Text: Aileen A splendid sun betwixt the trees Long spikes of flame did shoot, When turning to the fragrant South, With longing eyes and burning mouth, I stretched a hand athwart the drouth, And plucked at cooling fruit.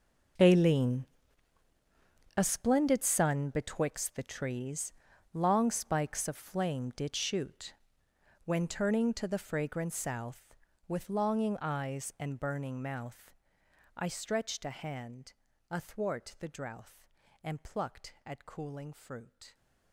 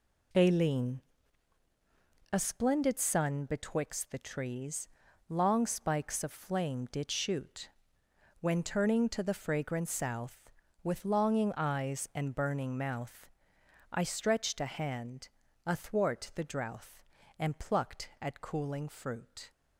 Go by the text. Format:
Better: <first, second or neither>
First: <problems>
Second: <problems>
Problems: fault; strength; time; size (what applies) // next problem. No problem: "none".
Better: second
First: gets quieter; strong; throughout; 16.5 dB // pauses between "Aileen" and "A"; strong; at 1.0 s; 1.3 s long // pauses between "trees" and "Long"; at 4.9 s; 0.40 s long // pauses between "hand" and "athwart"; at 15.3 s; 0.38 s long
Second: pauses between "Aileen" and "A"; strong; at 1.0 s; 1.3 s long // pauses between "trees" and "Long"; at 4.8 s; 0.40 s long // pauses between "hand" and "athwart"; at 15.2 s; 0.38 s long